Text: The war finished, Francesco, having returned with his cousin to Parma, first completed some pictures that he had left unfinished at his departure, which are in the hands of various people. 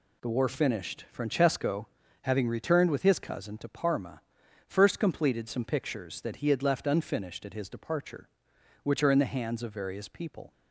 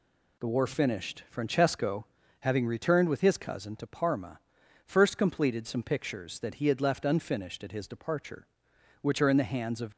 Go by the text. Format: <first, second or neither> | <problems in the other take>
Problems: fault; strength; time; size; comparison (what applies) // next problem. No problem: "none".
first | stops before "various people"; at 9.9 s